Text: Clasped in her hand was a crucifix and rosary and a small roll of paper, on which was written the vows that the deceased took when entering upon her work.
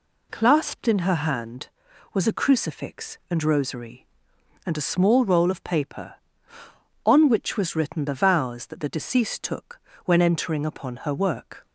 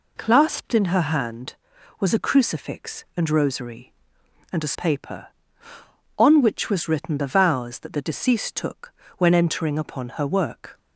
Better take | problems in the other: first | skips "small roll of"; at 4.7 s // pauses between "took" and "when"; slight; at 8.9 s; 0.26 s long; slight in the first

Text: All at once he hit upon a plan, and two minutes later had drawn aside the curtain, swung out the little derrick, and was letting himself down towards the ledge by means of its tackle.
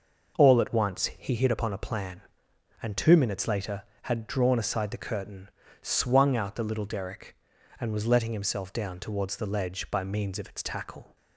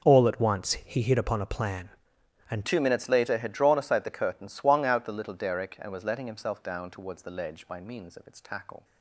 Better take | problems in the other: first | starts louder than the rest; until 1.1 s; 6.5 dB // changes voice at "two"; from 2.6 s on; 6.2 s long

